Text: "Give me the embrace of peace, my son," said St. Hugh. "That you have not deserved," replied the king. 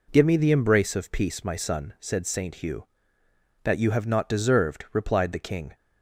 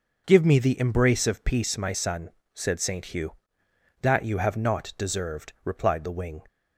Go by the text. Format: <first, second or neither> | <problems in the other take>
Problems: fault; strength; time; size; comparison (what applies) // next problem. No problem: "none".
first | says "wing" for "king"; at 6.1 s